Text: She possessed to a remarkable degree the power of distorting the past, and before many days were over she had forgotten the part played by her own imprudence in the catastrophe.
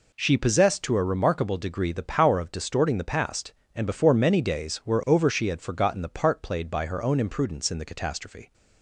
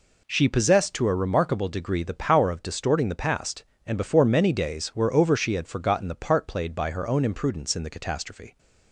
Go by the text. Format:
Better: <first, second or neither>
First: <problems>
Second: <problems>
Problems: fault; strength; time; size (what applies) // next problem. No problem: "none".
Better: neither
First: none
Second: none